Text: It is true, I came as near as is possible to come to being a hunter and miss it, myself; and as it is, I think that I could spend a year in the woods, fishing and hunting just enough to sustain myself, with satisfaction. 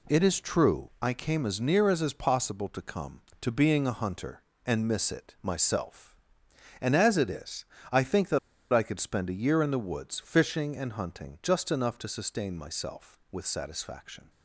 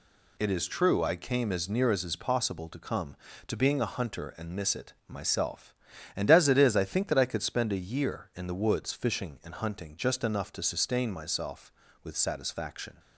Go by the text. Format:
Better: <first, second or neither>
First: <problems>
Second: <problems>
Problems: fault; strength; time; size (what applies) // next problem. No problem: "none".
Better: second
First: pauses between "that" and "I"; slight; at 8.3 s; 0.34 s long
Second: none